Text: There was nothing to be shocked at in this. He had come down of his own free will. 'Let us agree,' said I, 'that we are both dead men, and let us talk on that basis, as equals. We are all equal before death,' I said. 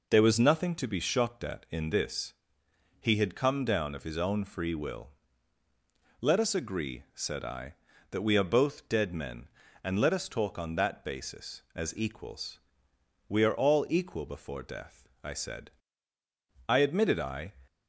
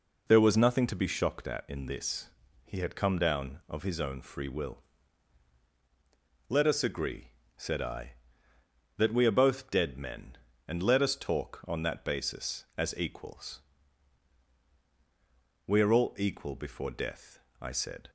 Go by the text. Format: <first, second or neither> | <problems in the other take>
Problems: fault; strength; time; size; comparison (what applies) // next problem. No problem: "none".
second | goes on to say "I admitted I"; noticeable; from 16.6 s on; 0.86 s long